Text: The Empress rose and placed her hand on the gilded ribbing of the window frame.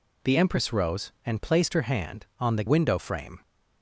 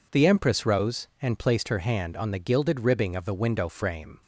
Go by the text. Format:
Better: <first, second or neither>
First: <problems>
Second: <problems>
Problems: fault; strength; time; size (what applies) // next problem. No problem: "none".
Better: second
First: skips "gilded ribbing of the"; at 2.6 s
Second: none